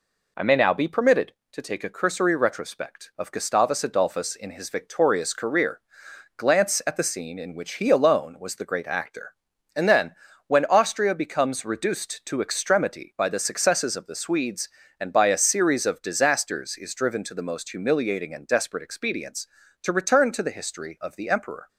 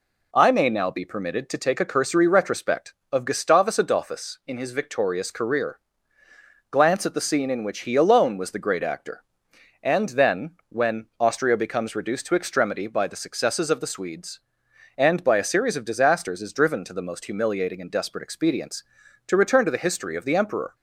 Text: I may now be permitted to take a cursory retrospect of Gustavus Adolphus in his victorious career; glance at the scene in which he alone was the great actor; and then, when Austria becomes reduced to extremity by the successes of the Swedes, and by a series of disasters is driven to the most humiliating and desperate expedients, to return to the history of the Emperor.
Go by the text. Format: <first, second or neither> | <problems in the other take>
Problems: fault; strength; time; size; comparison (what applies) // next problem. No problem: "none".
neither | none